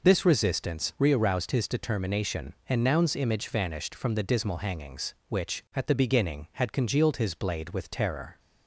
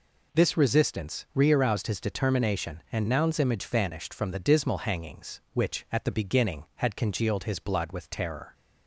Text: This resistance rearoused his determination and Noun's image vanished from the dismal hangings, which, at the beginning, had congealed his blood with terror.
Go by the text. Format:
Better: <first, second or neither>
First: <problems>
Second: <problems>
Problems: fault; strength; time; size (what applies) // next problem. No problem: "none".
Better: second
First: says "blade" for "blood"; at 7.3 s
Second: none